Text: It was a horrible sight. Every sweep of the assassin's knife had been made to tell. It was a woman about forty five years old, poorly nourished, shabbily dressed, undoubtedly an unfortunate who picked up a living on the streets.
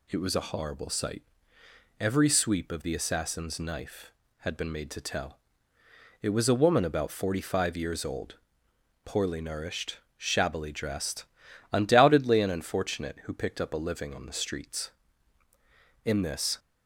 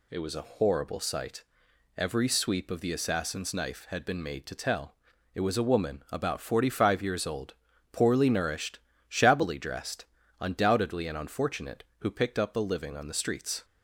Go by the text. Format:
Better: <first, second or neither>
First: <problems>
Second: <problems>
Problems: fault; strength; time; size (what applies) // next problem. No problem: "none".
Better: second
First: goes on to say "In this"; from 16.0 s on; 0.54 s long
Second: none